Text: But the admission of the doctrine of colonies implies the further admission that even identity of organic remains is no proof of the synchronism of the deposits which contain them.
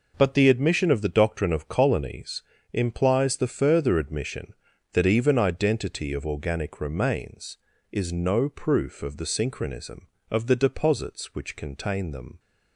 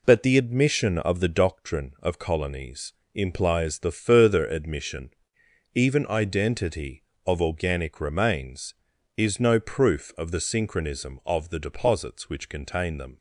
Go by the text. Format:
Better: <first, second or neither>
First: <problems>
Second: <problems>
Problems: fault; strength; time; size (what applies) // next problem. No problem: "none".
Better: first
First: pauses between "colonies" and "implies"; slight; at 2.4 s; 0.30 s long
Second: pauses between "colonies" and "implies"; slight; at 2.9 s; 0.22 s long // skips "that"; at 5.4 s